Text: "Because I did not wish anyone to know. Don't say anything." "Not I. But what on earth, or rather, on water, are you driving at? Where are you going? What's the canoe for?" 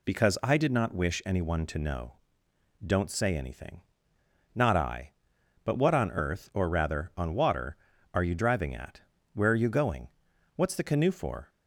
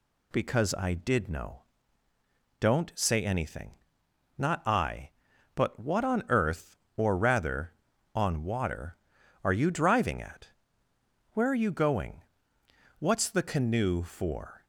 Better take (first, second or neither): first